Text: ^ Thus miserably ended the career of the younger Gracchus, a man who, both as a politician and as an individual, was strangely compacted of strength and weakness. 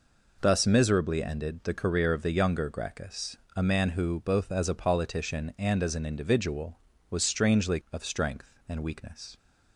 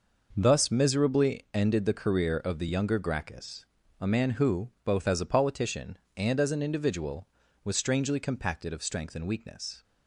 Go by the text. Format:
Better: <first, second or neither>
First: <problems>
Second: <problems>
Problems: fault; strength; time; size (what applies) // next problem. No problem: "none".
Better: second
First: skips "compacted"; at 7.8 s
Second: none